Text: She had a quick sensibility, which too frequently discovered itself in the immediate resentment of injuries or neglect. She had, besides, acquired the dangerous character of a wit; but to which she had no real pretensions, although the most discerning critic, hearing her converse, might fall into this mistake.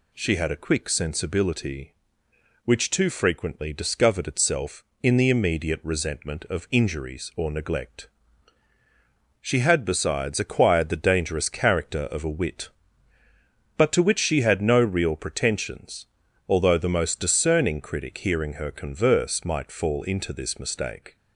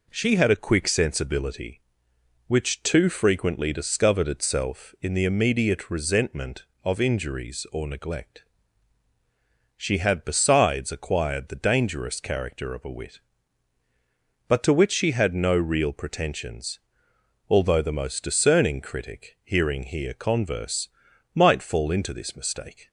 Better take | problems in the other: first | says "here" for "her"; at 19.8 s

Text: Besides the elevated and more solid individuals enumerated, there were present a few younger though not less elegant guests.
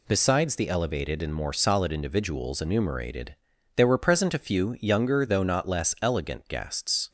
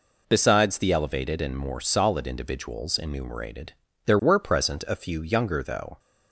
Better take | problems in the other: first | stops before "not less elegant guests"; at 5.9 s

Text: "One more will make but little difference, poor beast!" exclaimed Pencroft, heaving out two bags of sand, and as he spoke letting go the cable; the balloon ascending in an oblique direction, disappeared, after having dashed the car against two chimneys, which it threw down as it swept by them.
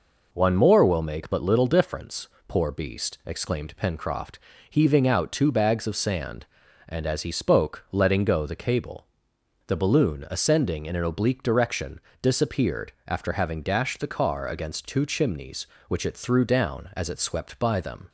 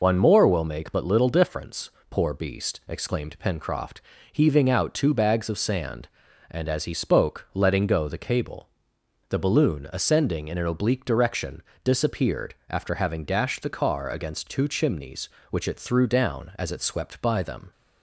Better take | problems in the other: first | loses the start of "One"; at 0.0 s; 65 ms

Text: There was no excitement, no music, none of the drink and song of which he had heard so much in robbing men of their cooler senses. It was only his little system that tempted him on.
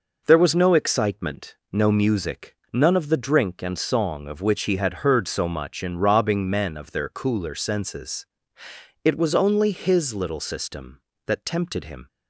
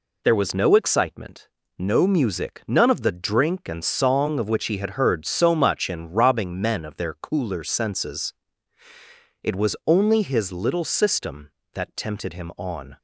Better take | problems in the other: second | stops before "on"; at 12.0 s

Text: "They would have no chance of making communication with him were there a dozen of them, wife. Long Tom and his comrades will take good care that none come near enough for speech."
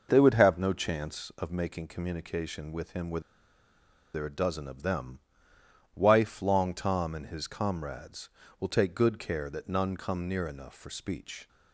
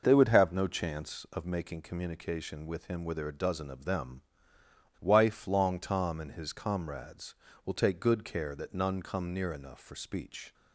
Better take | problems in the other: second | pauses between "were" and "there"; noticeable; at 3.1 s; 0.94 s long

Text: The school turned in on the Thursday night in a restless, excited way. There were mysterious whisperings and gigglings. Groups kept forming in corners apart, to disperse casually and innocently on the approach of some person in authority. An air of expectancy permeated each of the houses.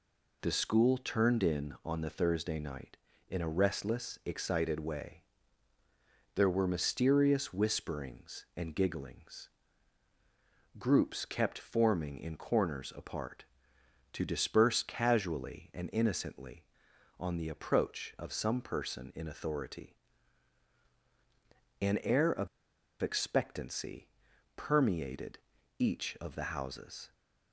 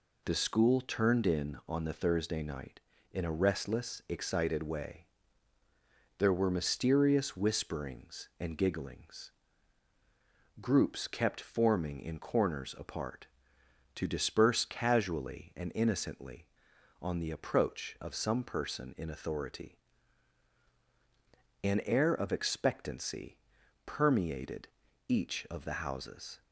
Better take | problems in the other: second | pauses between "of" and "expectancy"; noticeable; at 22.4 s; 0.54 s long // pauses between "expectancy" and "permeated"; noticeable; at 24.0 s; 0.48 s long; noticeable in the second // pauses between "permeated" and "each"; at 25.3 s; 0.40 s long; also in the second

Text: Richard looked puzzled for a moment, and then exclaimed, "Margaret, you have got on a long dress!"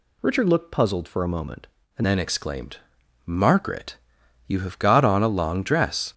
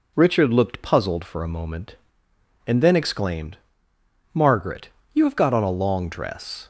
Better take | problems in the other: second | changes voice at "then"; from 2.0 s on; 4.1 s long

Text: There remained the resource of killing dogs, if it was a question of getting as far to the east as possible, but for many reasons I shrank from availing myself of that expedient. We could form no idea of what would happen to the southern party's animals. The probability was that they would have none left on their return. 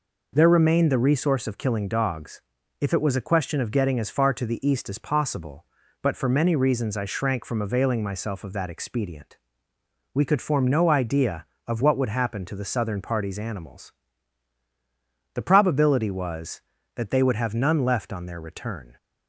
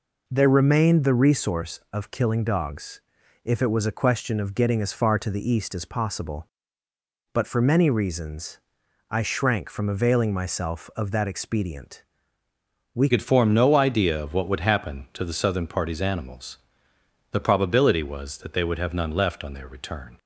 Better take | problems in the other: first | pauses between "reasons" and "I"; noticeable; at 8.5 s; 0.50 s long // changes voice at "could"; from 13.0 s on; 7.1 s long

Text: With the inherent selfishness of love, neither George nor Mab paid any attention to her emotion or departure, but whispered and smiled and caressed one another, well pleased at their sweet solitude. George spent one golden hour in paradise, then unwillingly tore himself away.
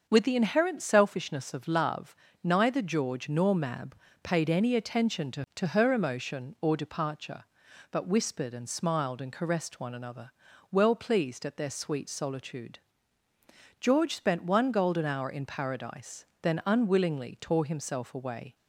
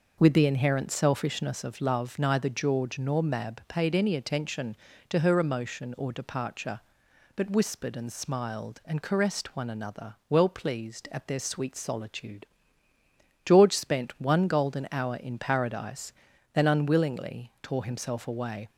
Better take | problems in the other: second | starts louder than the rest; until 1.1 s; 6.5 dB // pauses between "Mab" and "paid"; slight; at 3.9 s; 0.30 s long // says "to" twice; at 5.5 s

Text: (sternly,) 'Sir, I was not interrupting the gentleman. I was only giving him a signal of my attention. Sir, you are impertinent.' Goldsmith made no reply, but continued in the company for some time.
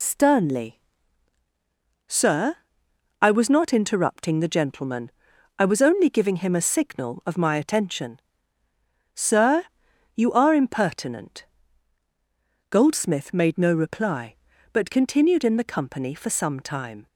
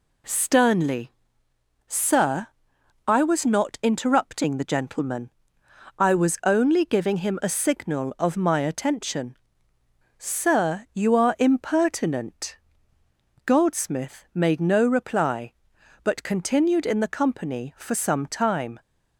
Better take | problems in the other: second | loses the start of "sternly"; at 0.0 s; 50 ms

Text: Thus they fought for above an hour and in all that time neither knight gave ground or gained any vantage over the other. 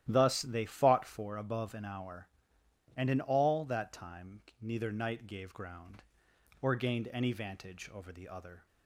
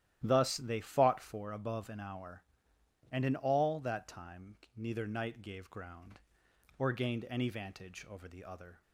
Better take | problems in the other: neither | starts louder than the rest; strong; the same in both // pauses between "time" and "neither"; slight; the same in both

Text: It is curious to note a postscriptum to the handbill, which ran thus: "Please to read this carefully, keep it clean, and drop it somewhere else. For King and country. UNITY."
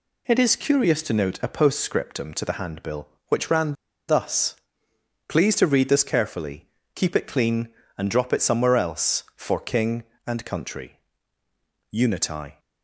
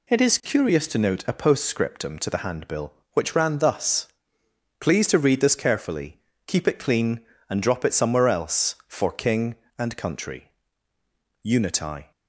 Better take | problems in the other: second | pauses between "ran" and "thus"; slight; at 3.7 s; 0.34 s long

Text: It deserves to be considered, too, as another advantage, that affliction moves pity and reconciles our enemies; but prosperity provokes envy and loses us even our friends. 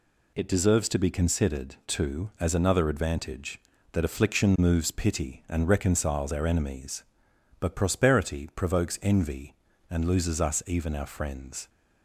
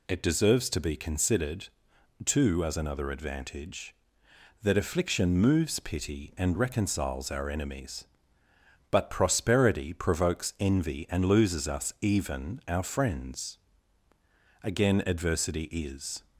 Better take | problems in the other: first | goes on to say "Again adversity is"; from 14.6 s on; 1.5 s long

